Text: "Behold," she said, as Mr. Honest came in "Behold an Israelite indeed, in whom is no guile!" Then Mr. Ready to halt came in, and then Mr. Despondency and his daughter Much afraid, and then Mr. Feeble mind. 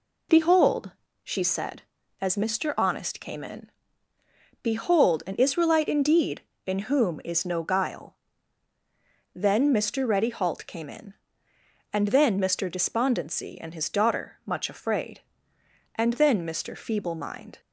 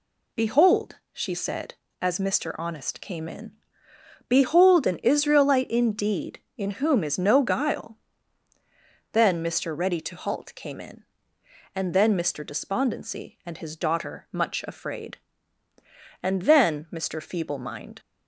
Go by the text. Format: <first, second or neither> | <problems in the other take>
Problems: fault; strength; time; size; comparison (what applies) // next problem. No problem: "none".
second | pauses between "in" and "Behold"; noticeable; at 3.6 s; 0.92 s long; noticeable in the second // skips "to"; at 10.2 s